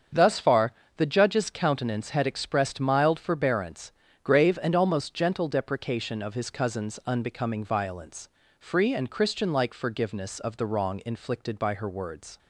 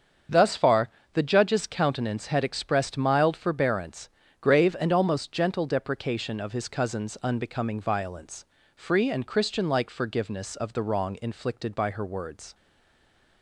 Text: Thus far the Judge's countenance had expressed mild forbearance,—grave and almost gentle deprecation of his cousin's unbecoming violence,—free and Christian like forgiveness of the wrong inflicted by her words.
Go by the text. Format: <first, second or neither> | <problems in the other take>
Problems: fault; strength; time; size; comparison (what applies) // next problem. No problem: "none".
first | starts louder than the rest; strong; until 1.5 s; 7 dB; strong in the first // pauses between "far" and "the"; slight; at 0.8 s; 0.26 s long; slight in the first // stays silent after the last word; slight; from 12.5 s on; 0.9 s long